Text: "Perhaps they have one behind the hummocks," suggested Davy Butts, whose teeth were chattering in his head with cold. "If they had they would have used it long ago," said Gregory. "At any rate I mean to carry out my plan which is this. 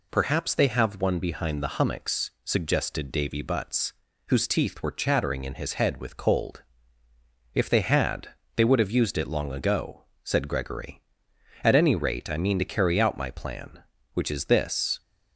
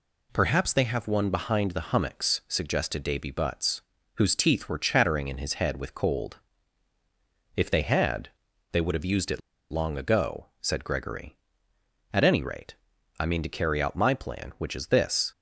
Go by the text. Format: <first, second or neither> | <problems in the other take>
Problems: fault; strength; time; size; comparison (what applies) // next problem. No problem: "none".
first | pauses between "had" and "they"; at 8.2 s; 0.42 s long; slight in the first // pauses between "it" and "long"; slight; at 9.3 s; 0.30 s long // pauses between "rate" and "I"; at 12.7 s; 0.42 s long